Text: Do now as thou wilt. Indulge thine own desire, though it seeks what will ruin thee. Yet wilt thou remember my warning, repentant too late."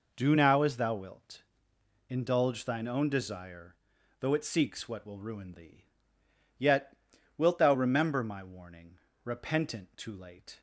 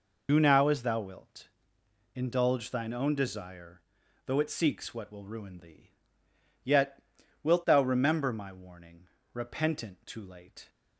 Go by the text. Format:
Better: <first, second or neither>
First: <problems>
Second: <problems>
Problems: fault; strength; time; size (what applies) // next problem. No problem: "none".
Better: first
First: pauses between "Yet" and "wilt"; at 6.9 s; 0.44 s long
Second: loses the start of "Do"; at 0.2 s; 100 ms // pauses between "Yet" and "wilt"; at 6.9 s; 0.44 s long